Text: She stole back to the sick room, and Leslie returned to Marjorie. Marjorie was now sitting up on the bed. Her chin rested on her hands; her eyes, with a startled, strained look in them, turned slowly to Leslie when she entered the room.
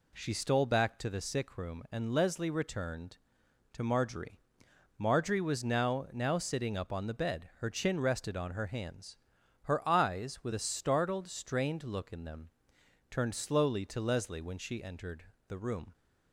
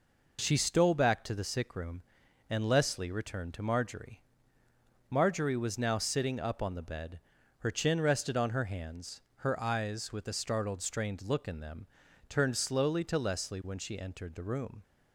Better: second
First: says "now" twice; at 6.1 s // pauses between "entered" and "the"; slight; at 15.2 s; 0.20 s long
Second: none

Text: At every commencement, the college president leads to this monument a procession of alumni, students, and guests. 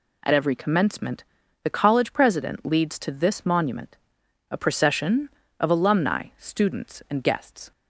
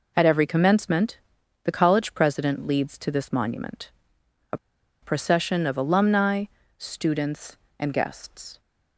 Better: first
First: pauses between "monument" and "a"; noticeable; at 3.9 s; 0.54 s long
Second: pauses between "monument" and "a"; noticeable; at 3.8 s; 0.62 s long // pauses between "a" and "procession"; at 4.5 s; 0.44 s long

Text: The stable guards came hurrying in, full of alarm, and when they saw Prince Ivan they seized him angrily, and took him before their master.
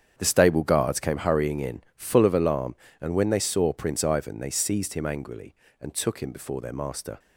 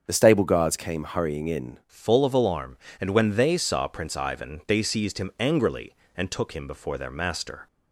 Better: first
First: starts louder than the rest; strong; until 1.1 s; 8 dB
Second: starts louder than the rest; until 1.0 s; 7 dB // changes voice at "full"; from 1.8 s on; 5.8 s long

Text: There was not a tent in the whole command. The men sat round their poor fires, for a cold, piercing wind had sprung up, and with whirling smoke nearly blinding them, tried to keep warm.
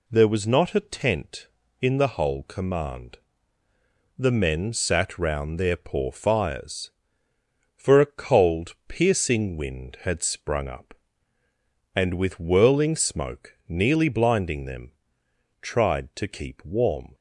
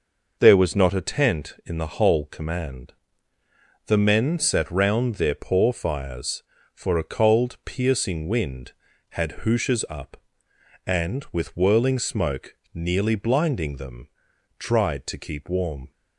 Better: first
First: none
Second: says "hooshes" for "sprung"; at 9.4 s // pauses between "smoke" and "nearly"; slight; at 12.5 s; 0.18 s long

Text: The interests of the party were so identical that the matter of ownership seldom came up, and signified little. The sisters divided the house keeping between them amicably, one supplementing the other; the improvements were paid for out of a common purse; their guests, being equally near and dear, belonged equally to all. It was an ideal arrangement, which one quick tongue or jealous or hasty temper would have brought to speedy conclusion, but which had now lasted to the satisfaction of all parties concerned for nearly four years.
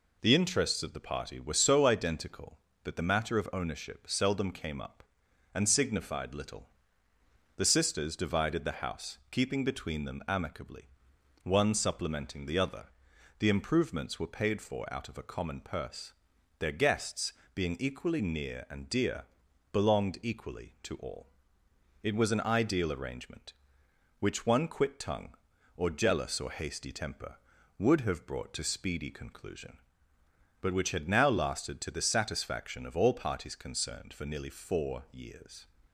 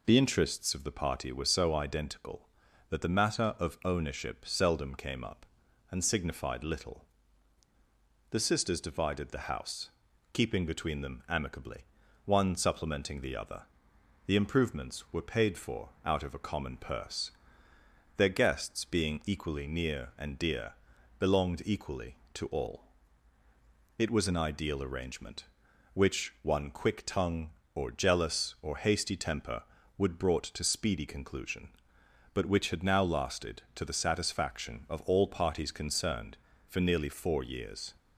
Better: first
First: none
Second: pauses between "house" and "keeping"; at 9.8 s; 0.44 s long // skips "have"; at 30.1 s

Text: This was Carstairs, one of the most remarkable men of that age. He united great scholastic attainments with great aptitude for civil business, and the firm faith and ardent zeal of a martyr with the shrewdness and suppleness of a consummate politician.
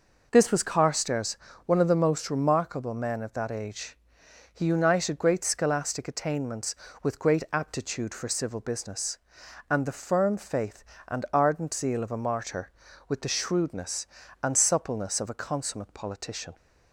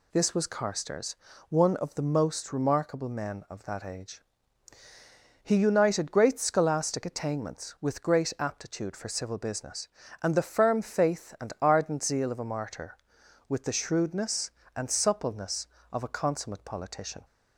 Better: neither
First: none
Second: none

